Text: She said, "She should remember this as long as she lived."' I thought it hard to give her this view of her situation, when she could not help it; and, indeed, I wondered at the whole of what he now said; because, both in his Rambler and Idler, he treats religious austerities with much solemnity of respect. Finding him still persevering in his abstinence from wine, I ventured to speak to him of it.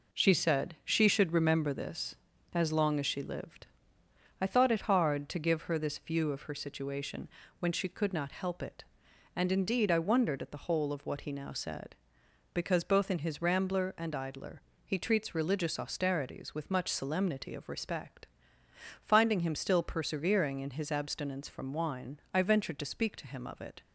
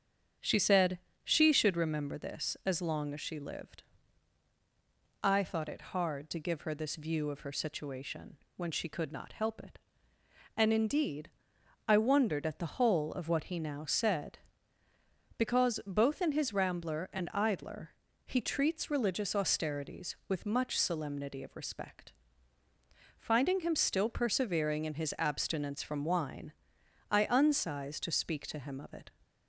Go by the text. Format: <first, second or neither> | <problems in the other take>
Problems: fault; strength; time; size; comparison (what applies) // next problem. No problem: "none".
first | starts louder than the rest; strong; until 1.6 s; 7.5 dB // says "unsized" for "ventured"; at 27.2 s